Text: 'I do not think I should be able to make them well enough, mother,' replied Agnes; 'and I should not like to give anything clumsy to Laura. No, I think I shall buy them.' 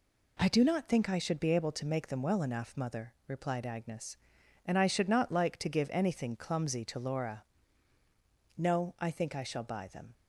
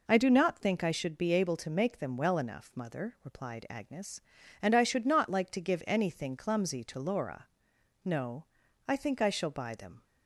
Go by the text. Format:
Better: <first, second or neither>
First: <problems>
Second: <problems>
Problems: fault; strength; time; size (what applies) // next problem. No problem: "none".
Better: neither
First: none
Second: none